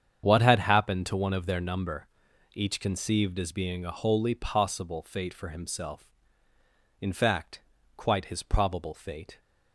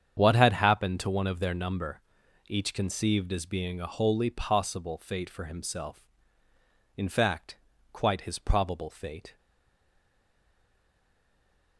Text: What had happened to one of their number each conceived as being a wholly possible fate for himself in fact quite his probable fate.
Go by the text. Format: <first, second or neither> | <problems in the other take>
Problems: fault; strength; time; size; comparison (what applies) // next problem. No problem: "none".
first | starts louder than the rest; strong; until 1.1 s; 8 dB; strong in the first // pauses between "number" and "each"; noticeable; at 2.0 s; 0.48 s long; noticeable in the first // pauses between "fact" and "quite"; slight; at 7.5 s; 0.36 s long; slight in the first // stays silent after the last word; from 9.3 s on; 2.4 s long